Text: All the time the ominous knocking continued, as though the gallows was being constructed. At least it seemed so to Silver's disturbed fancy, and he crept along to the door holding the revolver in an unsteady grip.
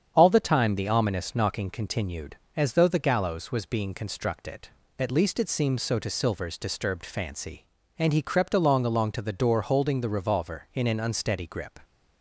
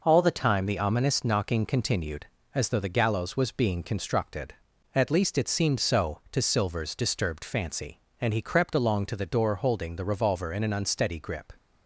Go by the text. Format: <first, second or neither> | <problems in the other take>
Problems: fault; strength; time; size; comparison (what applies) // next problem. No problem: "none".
second | starts louder than the rest; strong; until 1.1 s; 8 dB // says "along" twice; at 8.8 s